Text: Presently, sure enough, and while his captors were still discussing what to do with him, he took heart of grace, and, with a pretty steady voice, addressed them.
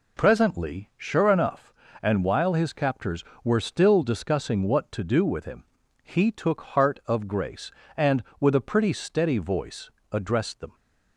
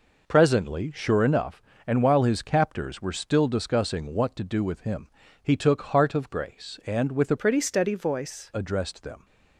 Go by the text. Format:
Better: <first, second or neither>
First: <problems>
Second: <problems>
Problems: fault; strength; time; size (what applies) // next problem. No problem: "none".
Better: first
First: none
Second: changes voice from "pretty" to "voice"; from 7.3 to 8.5 s; 1.2 s long